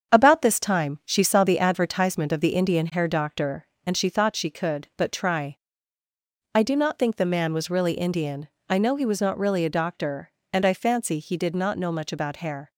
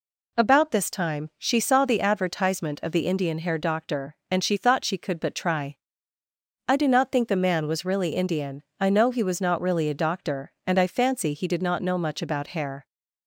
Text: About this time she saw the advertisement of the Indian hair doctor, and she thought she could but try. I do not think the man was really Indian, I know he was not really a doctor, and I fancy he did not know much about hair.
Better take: second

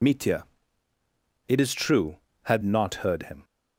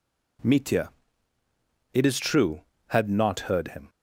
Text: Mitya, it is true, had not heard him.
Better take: second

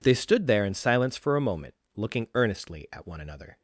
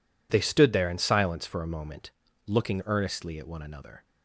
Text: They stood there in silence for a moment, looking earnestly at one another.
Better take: neither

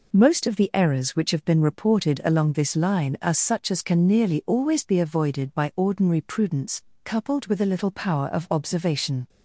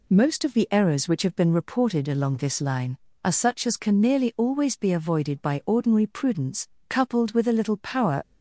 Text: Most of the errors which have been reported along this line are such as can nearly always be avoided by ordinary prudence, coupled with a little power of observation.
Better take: first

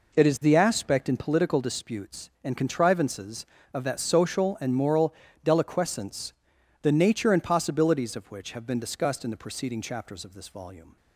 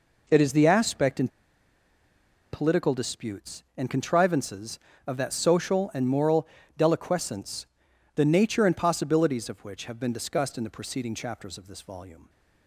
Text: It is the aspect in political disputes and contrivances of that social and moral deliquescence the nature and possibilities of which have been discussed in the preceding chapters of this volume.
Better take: first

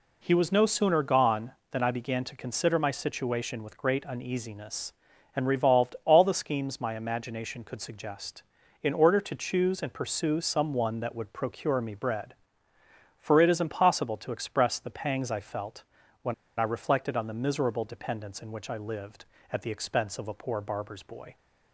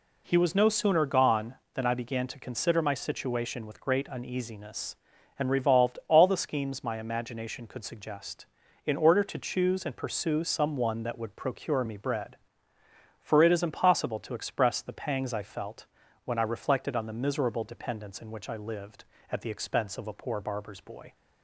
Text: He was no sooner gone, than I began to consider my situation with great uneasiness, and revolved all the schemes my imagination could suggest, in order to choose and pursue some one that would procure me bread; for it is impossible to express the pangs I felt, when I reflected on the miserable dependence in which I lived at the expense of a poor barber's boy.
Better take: second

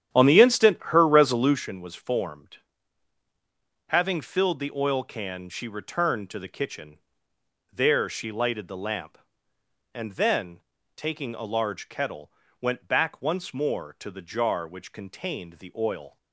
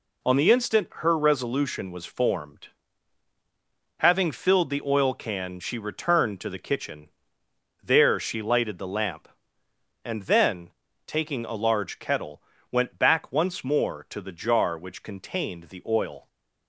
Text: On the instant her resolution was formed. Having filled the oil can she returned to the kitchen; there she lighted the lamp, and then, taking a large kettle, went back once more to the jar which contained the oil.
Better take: second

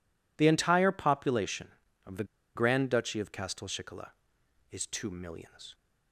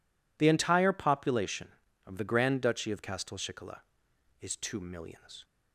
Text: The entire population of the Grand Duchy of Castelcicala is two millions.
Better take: second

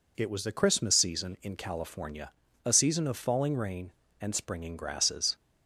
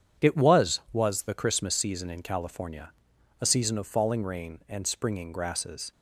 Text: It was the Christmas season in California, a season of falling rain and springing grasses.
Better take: first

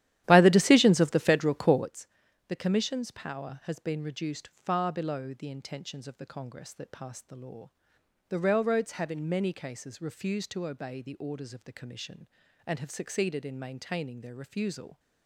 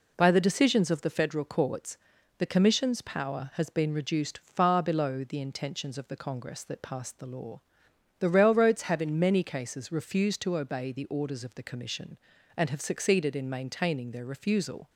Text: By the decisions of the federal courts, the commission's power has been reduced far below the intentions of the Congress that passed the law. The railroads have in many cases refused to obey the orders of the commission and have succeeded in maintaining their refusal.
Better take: second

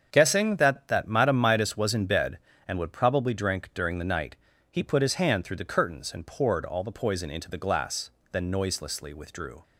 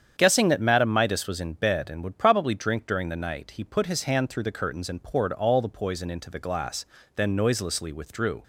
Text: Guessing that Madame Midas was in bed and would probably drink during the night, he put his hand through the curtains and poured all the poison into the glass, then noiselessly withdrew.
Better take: second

